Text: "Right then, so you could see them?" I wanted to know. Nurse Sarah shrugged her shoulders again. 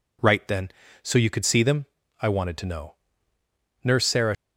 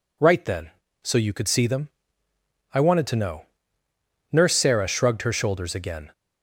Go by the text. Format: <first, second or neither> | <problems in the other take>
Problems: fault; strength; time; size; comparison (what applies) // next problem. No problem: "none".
second | stops before "shrugged her shoulders again"; at 4.3 s